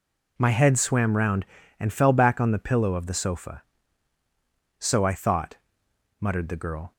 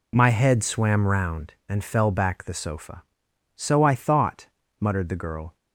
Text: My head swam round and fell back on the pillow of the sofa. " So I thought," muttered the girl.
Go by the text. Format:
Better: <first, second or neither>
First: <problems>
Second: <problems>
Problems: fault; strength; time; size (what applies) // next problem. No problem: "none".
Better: first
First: none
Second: skips "on the pillow of"; at 2.4 s